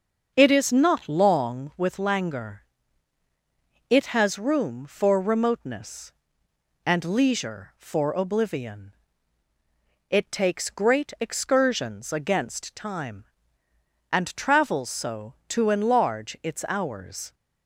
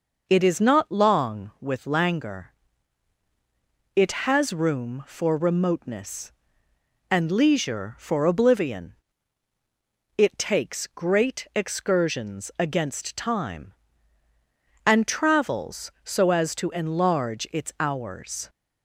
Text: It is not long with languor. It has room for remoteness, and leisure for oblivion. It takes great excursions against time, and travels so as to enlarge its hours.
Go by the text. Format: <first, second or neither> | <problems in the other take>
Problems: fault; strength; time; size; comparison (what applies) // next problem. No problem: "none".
second | starts louder than the rest; until 1.3 s; 6.5 dB // skips "as"; at 15.4 s